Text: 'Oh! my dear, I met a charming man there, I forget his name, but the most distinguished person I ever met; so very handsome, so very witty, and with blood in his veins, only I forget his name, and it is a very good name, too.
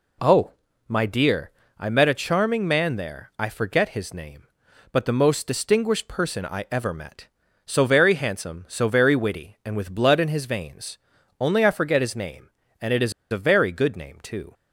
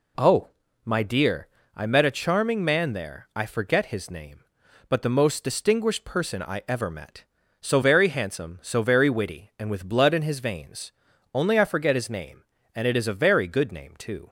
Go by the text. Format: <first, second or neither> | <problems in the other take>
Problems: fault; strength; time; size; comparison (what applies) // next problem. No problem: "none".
second | pauses between "is" and "a"; slight; at 13.1 s; 0.18 s long